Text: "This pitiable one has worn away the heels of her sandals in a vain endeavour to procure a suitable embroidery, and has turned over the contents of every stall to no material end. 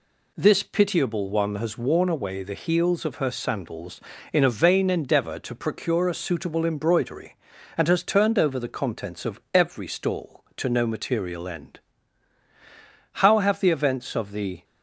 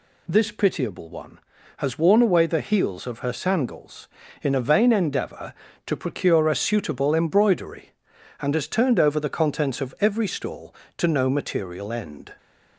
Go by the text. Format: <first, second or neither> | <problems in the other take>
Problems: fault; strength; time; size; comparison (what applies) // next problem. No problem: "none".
second | goes on to say "How have the events of the"; from 13.1 s on; 1.4 s long